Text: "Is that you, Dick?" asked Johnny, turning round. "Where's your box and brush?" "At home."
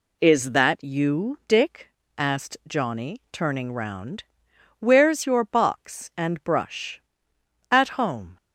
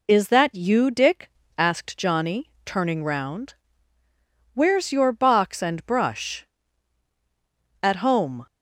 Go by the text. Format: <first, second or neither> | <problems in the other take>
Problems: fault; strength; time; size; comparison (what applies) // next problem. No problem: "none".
neither | none